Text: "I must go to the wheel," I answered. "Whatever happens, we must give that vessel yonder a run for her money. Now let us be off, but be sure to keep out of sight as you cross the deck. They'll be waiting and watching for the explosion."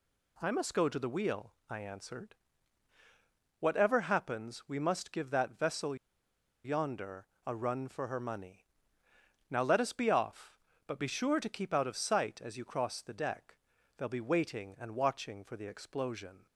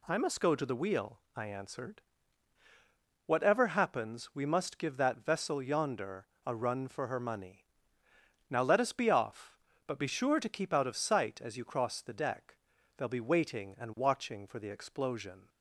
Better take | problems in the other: second | pauses between "vessel" and "yonder"; noticeable; at 5.9 s; 0.69 s long // pauses between "yonder" and "a"; slight; at 7.2 s; 0.20 s long; slight in the second

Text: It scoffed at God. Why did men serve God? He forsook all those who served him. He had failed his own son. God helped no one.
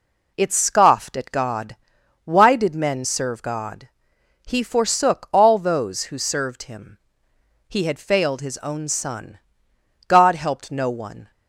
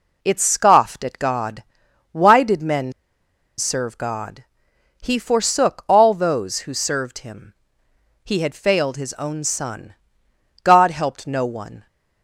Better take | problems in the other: first | pauses between "men" and "serve"; noticeable; at 2.9 s; 0.65 s long

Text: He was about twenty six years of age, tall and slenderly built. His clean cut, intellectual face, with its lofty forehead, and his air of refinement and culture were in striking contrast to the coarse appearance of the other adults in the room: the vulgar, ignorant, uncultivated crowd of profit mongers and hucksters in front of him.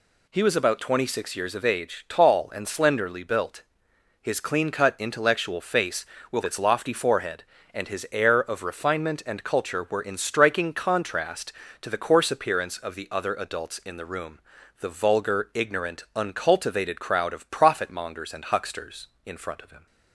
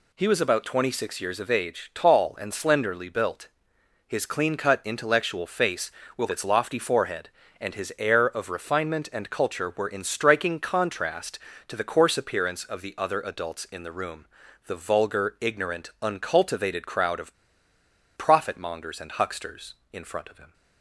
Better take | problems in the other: first | pauses between "of" and "profit"; noticeable; at 17.3 s; 0.84 s long

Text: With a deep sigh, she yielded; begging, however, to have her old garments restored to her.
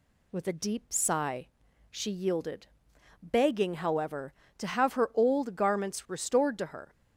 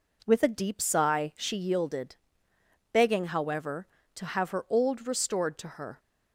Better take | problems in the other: first | skips "garments"; at 5.0 s

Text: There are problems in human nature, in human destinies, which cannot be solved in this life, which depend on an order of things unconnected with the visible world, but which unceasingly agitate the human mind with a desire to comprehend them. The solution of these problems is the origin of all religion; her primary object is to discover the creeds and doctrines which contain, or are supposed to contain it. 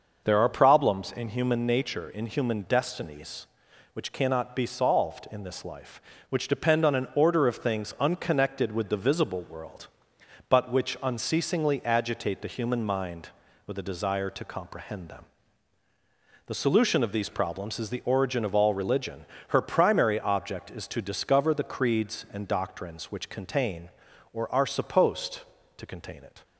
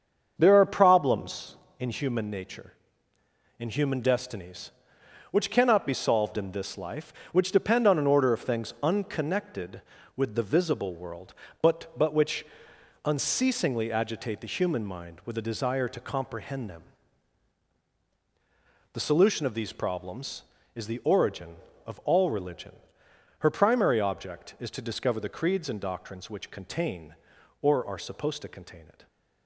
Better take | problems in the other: first | starts louder than the rest; until 1.3 s; 7 dB // says "but" twice; at 11.9 s // pauses between "which" and "unceasingly"; noticeable; at 12.4 s; 0.58 s long

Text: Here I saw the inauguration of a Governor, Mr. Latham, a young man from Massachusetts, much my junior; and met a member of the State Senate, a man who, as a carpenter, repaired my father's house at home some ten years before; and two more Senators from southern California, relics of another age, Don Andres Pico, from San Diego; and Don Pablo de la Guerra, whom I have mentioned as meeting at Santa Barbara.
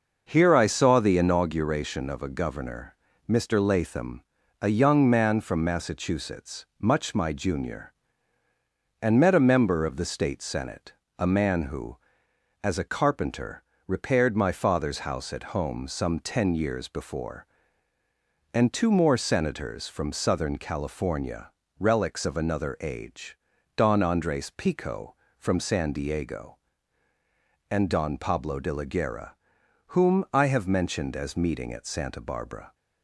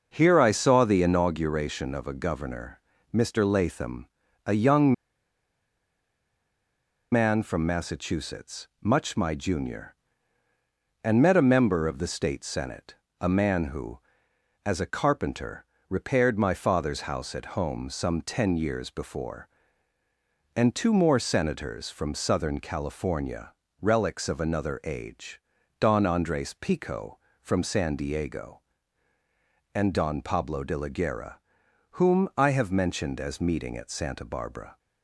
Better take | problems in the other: first | pauses between "young" and "man"; strong; at 4.9 s; 2.1 s long

